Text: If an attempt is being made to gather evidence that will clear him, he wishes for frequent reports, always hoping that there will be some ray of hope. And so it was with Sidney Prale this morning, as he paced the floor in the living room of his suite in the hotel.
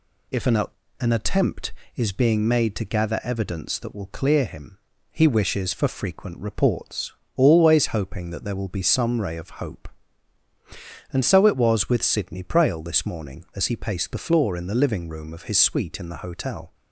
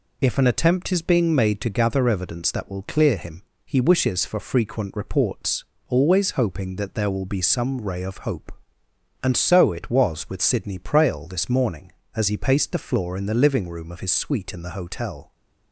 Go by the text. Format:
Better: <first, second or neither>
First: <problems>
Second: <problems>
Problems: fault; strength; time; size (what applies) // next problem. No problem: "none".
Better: second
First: says "an" twice; at 1.0 s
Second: none